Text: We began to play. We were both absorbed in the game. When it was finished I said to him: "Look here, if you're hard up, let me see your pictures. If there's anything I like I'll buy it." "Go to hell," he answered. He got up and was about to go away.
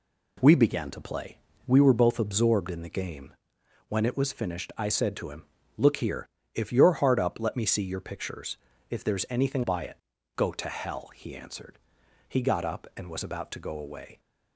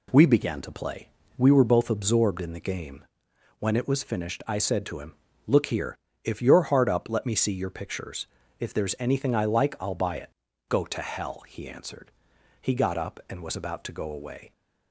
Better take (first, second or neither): second